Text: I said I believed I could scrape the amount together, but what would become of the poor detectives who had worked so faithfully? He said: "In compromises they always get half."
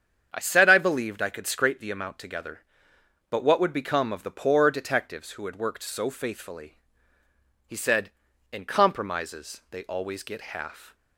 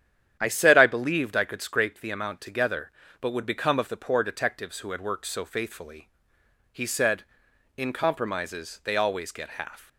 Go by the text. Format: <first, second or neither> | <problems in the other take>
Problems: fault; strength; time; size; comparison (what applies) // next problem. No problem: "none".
first | starts louder than the rest; strong; until 1.4 s; 10 dB; strong in the first // skips "what"; at 3.3 s